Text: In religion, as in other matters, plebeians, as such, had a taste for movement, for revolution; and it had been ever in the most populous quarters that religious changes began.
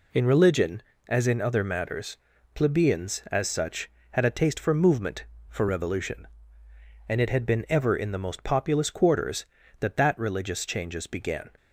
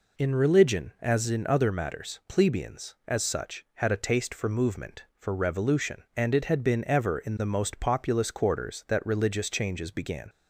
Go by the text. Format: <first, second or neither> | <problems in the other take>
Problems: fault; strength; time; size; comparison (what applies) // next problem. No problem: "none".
second | says "that" twice; at 9.9 s